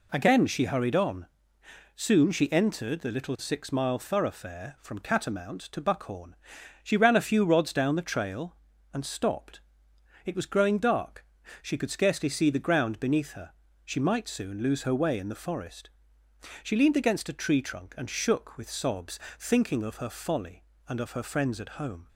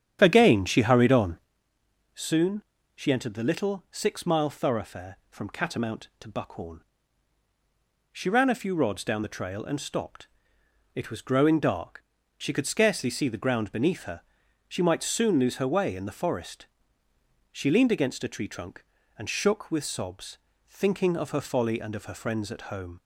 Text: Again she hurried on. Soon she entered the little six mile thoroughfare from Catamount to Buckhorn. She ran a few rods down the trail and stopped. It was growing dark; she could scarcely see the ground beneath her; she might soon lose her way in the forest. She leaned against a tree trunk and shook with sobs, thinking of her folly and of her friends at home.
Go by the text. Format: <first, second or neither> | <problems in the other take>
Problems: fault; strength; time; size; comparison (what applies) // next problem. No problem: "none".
first | starts louder than the rest; strong; until 1.5 s; 9 dB // pauses between "Soon" and "she"; slight; at 2.5 s; 0.34 s long